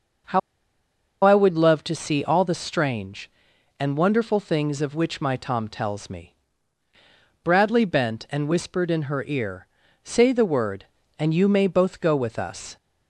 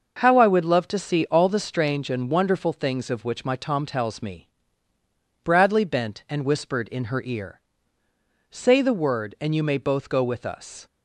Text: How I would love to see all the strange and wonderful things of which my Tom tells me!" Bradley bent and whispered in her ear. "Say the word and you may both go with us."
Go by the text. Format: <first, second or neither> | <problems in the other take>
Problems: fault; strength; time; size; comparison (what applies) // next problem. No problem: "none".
second | pauses between "How" and "I"; noticeable; at 0.3 s; 0.84 s long